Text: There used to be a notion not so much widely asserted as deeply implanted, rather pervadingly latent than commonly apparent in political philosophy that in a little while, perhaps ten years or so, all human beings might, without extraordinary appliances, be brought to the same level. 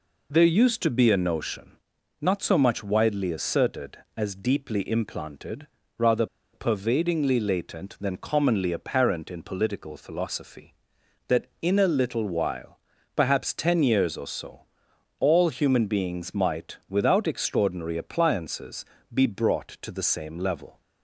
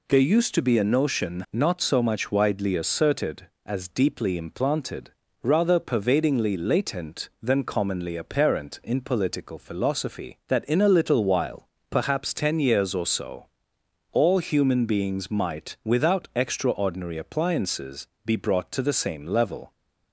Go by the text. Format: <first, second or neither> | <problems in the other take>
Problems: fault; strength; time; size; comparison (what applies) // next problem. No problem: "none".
second | pauses between "notion" and "not"; noticeable; at 1.7 s; 0.46 s long // pauses between "rather" and "pervadingly"; slight; at 6.2 s; 0.27 s long